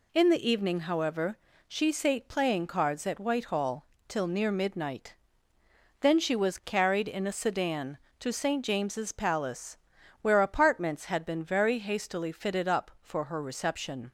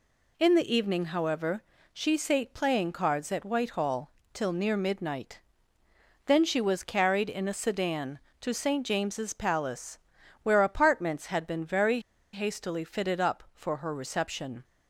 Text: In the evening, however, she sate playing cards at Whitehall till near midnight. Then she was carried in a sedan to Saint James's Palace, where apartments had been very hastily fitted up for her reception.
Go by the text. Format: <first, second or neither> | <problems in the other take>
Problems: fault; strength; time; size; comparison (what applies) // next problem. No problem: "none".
first | pauses between "Whitehall" and "till"; slight; at 4.1 s; 0.22 s long; slight in the first // pauses between "very" and "hastily"; slight; at 12.0 s; 0.32 s long